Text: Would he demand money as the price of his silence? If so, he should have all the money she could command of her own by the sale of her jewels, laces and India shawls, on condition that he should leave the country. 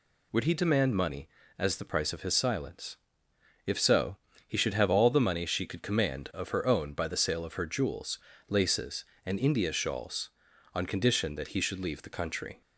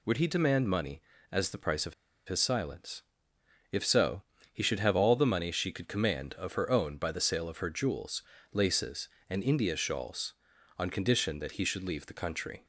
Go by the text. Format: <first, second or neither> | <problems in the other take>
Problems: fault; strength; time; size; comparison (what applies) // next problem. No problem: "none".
first | pauses between "of" and "his"; slight; at 1.9 s; 0.32 s long